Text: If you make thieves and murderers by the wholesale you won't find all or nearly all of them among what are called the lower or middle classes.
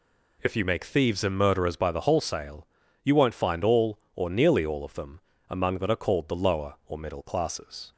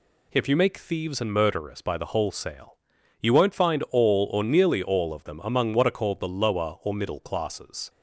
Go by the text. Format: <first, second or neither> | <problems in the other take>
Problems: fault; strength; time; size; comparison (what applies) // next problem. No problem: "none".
second | pauses between "wholesale" and "you"; slight; at 2.6 s; 0.36 s long; noticeable in the second // pauses between "them" and "among"; slight; at 5.1 s; 0.30 s long // says "that" for "what"; at 5.7 s